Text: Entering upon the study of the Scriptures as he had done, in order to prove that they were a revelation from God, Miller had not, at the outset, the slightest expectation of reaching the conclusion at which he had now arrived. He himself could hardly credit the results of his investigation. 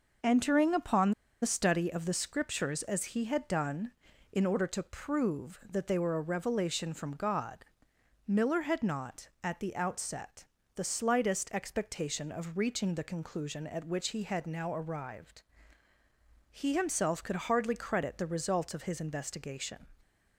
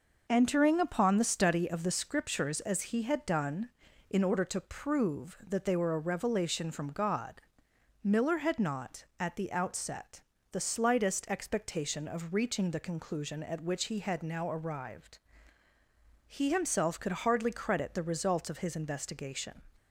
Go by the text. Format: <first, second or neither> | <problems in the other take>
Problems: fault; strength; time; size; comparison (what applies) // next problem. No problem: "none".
second | pauses between "upon" and "the"; slight; at 1.1 s; 0.31 s long